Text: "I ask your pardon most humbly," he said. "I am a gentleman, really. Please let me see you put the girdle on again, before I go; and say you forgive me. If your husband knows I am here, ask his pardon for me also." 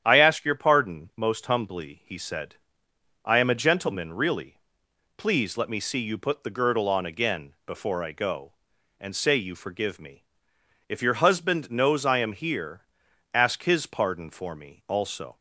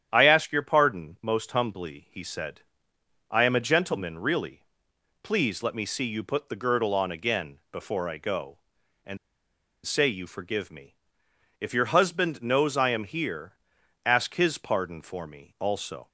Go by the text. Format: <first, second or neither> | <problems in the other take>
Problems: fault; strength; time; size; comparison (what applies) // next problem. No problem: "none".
first | starts louder than the rest; strong; until 1.1 s; 9.5 dB; strong in the first // pauses between "and" and "say"; noticeable; at 9.1 s; 0.67 s long